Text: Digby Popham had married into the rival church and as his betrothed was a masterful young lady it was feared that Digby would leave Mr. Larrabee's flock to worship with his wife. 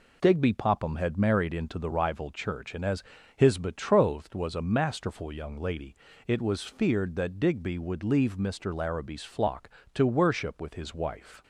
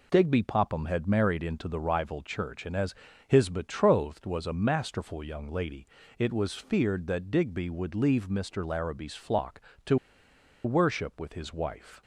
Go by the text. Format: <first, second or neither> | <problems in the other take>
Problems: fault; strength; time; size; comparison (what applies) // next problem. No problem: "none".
first | pauses between "as" and "his"; slight; at 2.9 s; 0.32 s long; slight in the first // pauses between "lady" and "it"; slight; at 5.8 s; 0.32 s long; slight in the first // pauses between "to" and "worship"; noticeable; at 9.9 s; 0.69 s long